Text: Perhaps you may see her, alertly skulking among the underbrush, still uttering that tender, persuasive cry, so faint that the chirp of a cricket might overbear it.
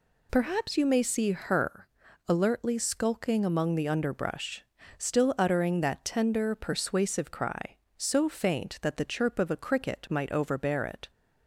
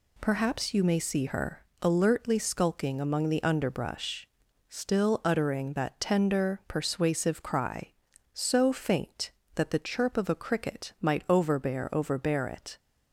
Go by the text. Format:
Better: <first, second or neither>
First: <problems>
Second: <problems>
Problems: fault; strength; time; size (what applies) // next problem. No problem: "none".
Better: first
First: none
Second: says "overbear" twice; at 11.9 s